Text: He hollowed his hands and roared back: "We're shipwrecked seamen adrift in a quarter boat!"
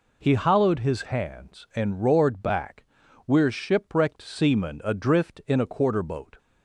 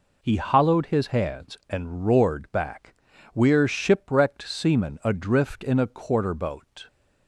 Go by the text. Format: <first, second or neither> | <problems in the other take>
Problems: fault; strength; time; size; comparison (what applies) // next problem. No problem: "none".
neither | none